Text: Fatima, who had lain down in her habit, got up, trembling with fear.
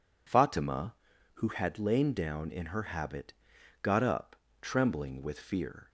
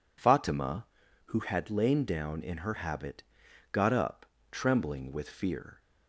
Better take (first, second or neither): neither